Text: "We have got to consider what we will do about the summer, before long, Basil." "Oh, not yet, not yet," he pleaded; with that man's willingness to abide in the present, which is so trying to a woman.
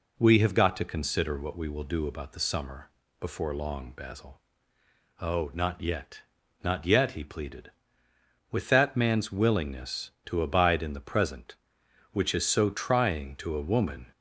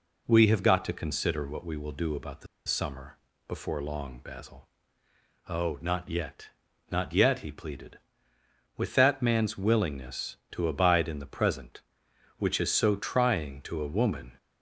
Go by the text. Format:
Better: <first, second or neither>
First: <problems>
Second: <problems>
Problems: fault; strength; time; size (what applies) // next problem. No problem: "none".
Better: first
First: none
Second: pauses between "the" and "summer"; slight; at 2.4 s; 0.20 s long